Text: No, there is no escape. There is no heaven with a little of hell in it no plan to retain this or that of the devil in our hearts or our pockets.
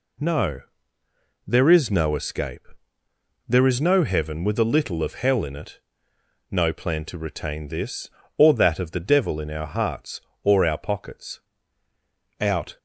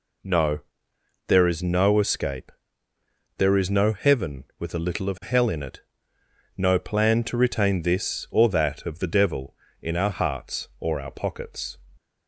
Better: second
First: pauses between "it" and "no"; noticeable; at 5.7 s; 0.70 s long // goes on to say "Out"; slight; from 12.3 s on; 0.38 s long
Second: pauses between "it" and "no"; noticeable; at 5.8 s; 0.74 s long

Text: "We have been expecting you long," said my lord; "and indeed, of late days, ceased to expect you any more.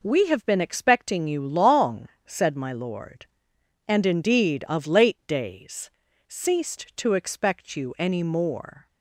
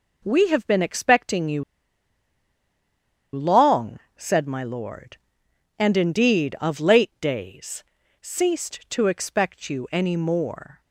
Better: first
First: none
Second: pauses between "you" and "long"; strong; at 1.6 s; 1.7 s long

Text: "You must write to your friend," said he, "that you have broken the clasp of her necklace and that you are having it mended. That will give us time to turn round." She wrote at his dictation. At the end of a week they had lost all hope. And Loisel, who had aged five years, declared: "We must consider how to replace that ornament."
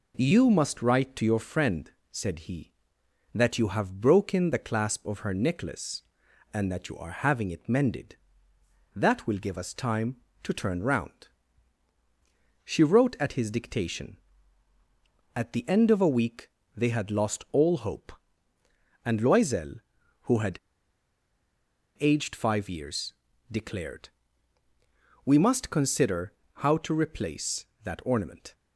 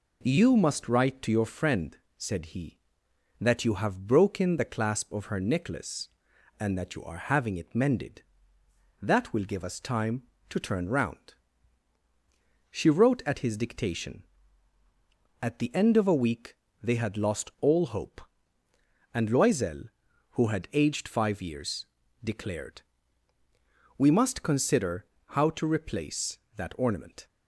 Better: second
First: pauses between "week" and "they"; slight; at 16.4 s; 0.24 s long // pauses between "had" and "aged"; strong; at 20.5 s; 1.4 s long // pauses between "consider" and "how"; slight; at 26.3 s; 0.22 s long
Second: pauses between "week" and "they"; slight; at 16.5 s; 0.24 s long // pauses between "consider" and "how"; slight; at 25.0 s; 0.22 s long

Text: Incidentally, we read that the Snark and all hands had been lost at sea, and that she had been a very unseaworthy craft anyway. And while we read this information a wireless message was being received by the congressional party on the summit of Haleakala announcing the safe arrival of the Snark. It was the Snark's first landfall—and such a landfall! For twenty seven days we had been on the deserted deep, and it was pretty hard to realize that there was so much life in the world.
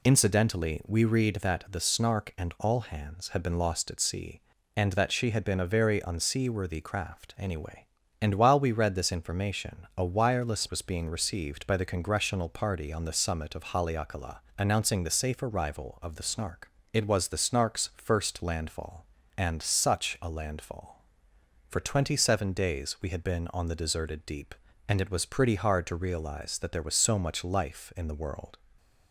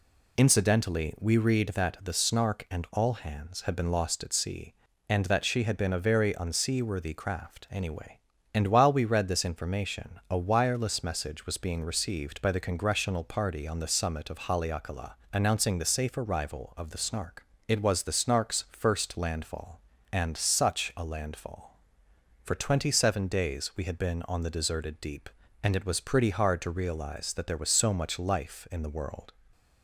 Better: second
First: skips "message"; at 10.6 s // pauses between "Haleakala" and "announcing"; slight; at 14.4 s; 0.16 s long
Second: pauses between "Haleakala" and "announcing"; slight; at 15.1 s; 0.16 s long

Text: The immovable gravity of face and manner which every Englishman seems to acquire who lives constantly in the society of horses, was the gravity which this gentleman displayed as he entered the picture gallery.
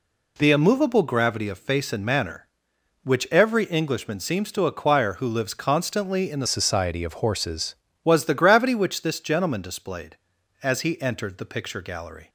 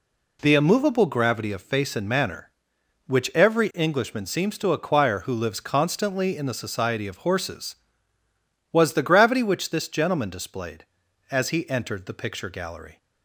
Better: second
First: changes voice from "society" to "horses"; from 6.4 to 7.7 s; 1.3 s long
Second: none

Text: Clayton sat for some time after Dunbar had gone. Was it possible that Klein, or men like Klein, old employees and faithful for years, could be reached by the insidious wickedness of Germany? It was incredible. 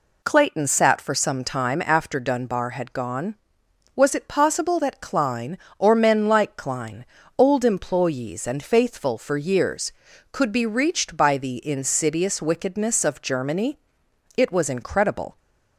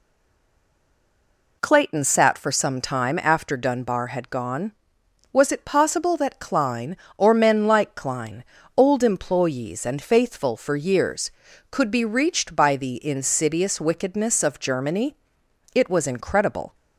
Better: first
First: none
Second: stays silent before the first word; noticeable; until 1.6 s; 1.6 s long

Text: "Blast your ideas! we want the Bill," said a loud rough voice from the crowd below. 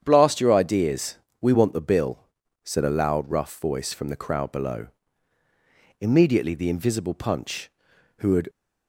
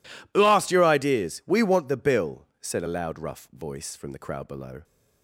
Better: second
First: starts louder than the rest; strong; until 1.0 s; 8 dB // goes on to say "Immediately the invisible Punch who had"; strong; from 5.9 s on; 2.5 s long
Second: none

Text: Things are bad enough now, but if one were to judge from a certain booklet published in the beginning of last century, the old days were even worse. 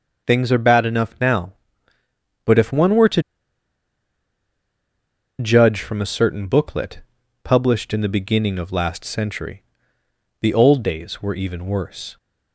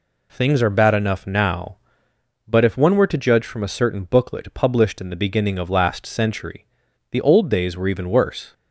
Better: second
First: pauses between "to" and "judge"; strong; at 3.2 s; 2.1 s long // pauses between "booklet" and "published"; at 7.0 s; 0.42 s long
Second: none

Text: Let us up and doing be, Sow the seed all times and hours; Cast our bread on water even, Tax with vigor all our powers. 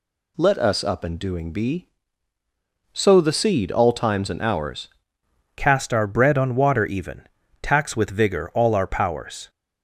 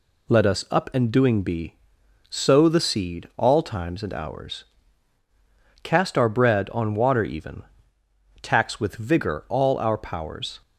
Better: second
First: changes voice at "Cast"; from 5.5 s on; 3.9 s long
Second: none

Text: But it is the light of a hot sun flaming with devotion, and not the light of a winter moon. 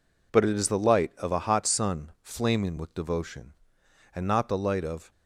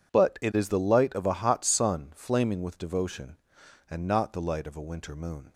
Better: second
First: stops before "a winter moon"; at 5.1 s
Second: none

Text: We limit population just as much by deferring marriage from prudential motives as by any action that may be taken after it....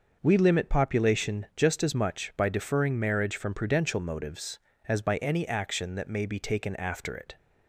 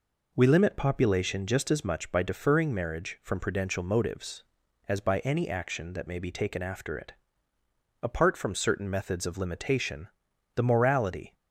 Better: first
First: none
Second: goes on to say "Apart from certain methods of limitation the morality"; strong; from 8.0 s on; 3.3 s long

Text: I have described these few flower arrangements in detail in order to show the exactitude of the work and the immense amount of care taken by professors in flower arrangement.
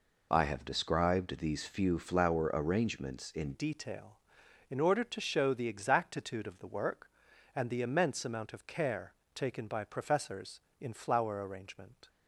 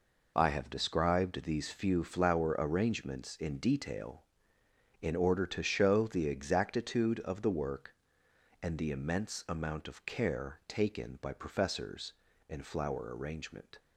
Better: second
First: changes voice at "detail"; from 3.5 s on; 8.5 s long // pauses between "care" and "taken"; slight; at 9.1 s; 0.22 s long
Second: none

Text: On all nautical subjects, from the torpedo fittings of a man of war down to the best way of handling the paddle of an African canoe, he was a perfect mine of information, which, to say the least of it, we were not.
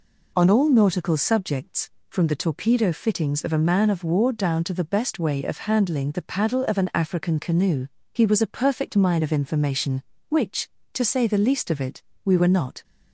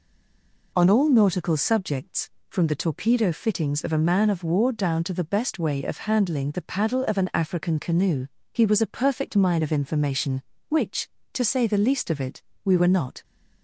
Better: first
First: none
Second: stays silent before the first word; slight; until 0.7 s; 0.7 s long

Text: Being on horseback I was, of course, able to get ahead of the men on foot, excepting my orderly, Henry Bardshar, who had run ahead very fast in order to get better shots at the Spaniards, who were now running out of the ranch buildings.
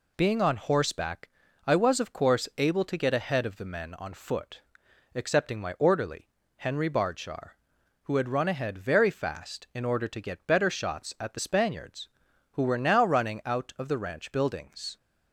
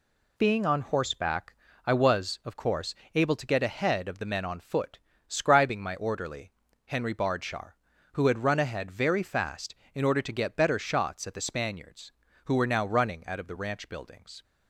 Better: first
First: pauses between "horseback" and "I"; slight; at 1.2 s; 0.36 s long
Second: pauses between "horseback" and "I"; slight; at 1.5 s; 0.32 s long // says "scribing" for "excepting"; at 5.2 s

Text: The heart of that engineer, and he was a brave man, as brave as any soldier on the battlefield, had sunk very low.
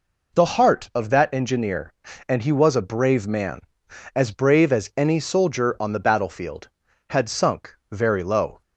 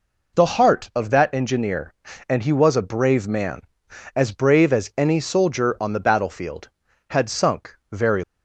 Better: first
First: pauses between "sunk" and "very"; slight; at 7.7 s; 0.16 s long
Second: pauses between "sunk" and "very"; slight; at 7.7 s; 0.16 s long // stops before "low"; at 8.2 s

